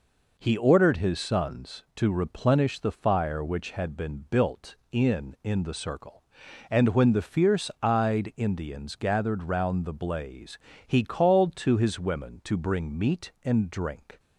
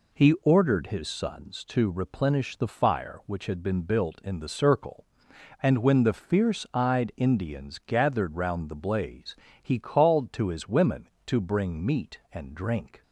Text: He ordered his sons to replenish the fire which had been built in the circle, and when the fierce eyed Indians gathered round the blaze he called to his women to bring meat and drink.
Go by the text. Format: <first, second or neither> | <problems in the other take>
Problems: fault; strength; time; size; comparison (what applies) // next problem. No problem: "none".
second | says "in" twice; at 5.4 s // pauses between "blaze" and "he"; slight; at 10.5 s; 0.26 s long; slight in the second